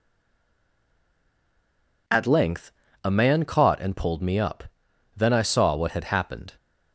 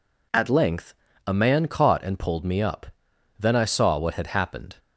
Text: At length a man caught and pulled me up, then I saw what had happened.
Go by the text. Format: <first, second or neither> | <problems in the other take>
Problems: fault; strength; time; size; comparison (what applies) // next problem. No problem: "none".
second | stays silent before the first word; noticeable; until 2.0 s; 2.0 s long // pauses between "length" and "a"; slight; at 2.7 s; 0.32 s long; slight in the second